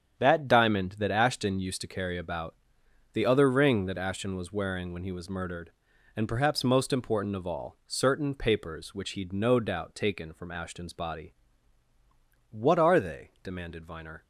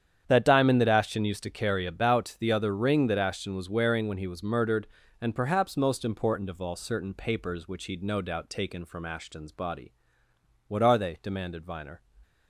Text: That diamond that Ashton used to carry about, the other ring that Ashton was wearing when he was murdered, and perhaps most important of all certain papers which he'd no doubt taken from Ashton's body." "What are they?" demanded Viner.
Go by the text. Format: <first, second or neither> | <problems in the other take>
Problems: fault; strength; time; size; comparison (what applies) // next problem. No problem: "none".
neither | starts louder than the rest; strong; the same in both